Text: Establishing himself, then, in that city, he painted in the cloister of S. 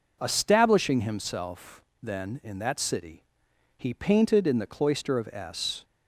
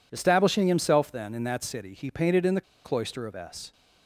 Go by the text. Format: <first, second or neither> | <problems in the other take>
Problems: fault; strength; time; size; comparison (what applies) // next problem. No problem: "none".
first | pauses between "the" and "cloister"; slight; at 2.6 s; 0.23 s long